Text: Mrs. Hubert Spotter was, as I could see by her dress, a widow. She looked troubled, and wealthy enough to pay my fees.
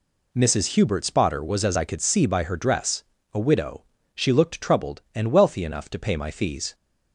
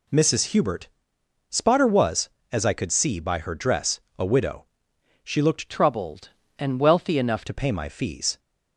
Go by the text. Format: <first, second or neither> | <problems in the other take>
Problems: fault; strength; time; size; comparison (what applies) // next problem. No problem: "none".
first | pauses between "Hubert" and "Spotter"; noticeable; at 0.8 s; 0.62 s long // changes voice from "troubled" to "enough"; from 5.6 to 7.4 s; 1.8 s long